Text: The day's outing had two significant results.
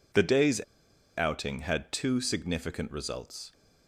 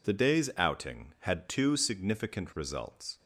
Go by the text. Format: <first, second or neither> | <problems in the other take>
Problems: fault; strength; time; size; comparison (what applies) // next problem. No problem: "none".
second | pauses between "day's" and "outing"; noticeable; at 0.5 s; 0.57 s long